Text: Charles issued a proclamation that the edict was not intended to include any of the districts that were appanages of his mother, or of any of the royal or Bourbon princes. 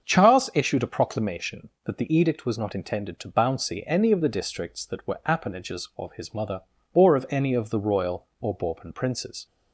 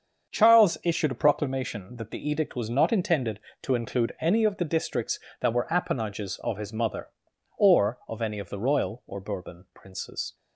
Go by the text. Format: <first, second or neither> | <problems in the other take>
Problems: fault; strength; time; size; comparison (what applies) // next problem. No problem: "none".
second | starts louder than the rest; until 1.1 s; 7 dB; also in the second // says "bouncy" for "include"; at 3.2 s